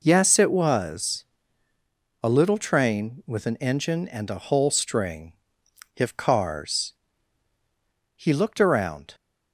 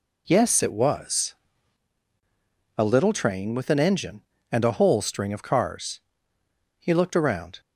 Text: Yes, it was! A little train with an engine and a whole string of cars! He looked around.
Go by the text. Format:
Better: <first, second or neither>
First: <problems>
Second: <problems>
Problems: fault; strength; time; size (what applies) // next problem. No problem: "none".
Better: second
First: says "if" for "of"; at 5.9 s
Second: none